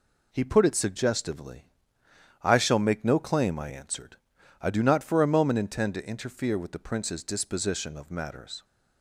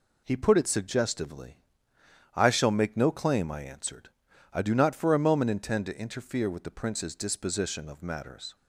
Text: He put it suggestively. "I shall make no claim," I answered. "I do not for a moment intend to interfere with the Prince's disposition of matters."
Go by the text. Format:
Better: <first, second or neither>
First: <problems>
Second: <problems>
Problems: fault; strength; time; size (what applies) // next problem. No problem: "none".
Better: neither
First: none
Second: none